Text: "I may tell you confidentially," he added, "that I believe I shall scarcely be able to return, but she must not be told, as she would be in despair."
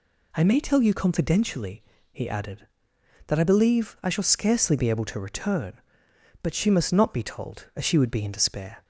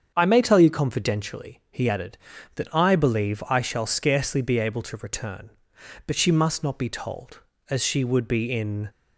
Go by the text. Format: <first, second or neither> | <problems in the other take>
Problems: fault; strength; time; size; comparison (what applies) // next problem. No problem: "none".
first | starts louder than the rest; strong; until 1.1 s; 7.5 dB // stops before "despair"; at 8.8 s